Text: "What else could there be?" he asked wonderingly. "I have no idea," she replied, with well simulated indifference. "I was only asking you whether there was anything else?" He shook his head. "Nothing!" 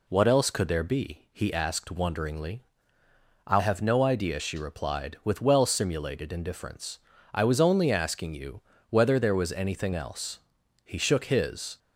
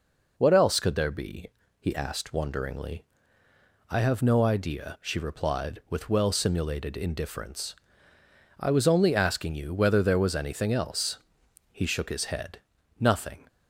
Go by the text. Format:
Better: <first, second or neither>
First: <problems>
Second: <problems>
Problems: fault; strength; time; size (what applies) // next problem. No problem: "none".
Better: second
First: pauses between "you" and "whether"; slight; at 8.6 s; 0.30 s long // stops before "head Nothing"; at 11.7 s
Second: none